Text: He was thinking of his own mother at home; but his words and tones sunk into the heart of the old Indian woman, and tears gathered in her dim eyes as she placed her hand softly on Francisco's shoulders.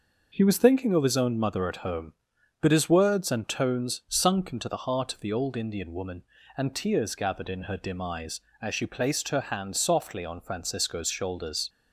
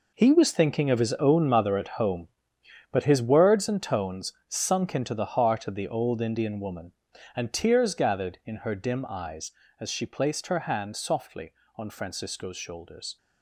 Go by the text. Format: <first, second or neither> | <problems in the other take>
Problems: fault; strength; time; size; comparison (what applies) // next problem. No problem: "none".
first | gets quieter; strong; throughout; 11.5 dB